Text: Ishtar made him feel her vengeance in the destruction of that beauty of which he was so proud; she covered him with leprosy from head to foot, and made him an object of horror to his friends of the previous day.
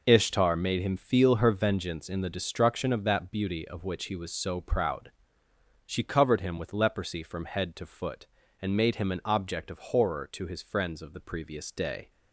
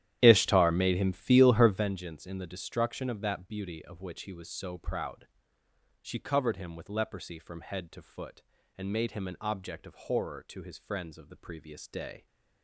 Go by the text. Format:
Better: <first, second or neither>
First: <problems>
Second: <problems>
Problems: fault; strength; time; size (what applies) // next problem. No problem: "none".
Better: first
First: none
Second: starts louder than the rest; strong; until 1.9 s; 12 dB